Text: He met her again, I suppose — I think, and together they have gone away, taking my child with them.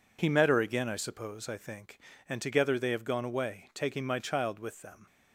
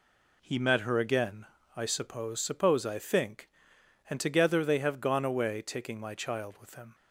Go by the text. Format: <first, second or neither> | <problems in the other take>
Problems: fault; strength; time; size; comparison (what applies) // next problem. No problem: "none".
first | says "suppose" twice; at 2.4 s